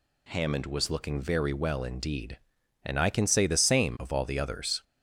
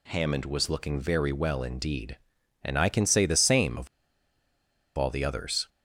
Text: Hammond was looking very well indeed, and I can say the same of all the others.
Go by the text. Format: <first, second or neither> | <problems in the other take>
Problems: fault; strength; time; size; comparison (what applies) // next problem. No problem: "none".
first | pauses between "of" and "all"; at 3.8 s; 1.1 s long